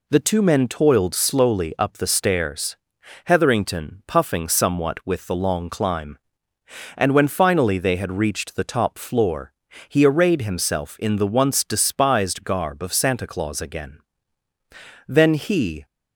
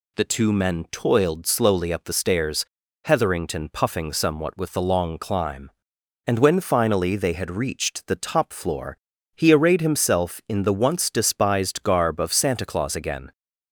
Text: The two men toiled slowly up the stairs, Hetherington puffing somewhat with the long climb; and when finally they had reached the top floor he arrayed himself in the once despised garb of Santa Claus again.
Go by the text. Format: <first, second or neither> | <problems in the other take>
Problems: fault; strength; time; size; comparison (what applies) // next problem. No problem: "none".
second | pauses between "floor" and "he"; at 9.5 s; 0.38 s long; also in the second // goes on to say "Then he"; noticeable; from 15.0 s on; 0.78 s long